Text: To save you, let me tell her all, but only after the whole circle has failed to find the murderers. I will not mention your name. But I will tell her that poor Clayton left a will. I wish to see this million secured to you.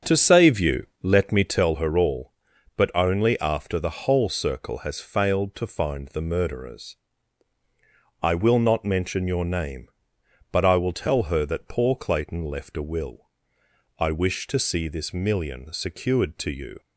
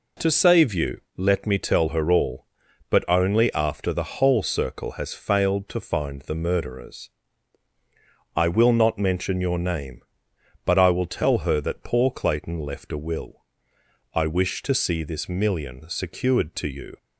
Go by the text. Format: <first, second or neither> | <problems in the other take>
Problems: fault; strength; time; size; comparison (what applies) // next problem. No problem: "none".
second | starts louder than the rest; strong; until 1.7 s; 7.5 dB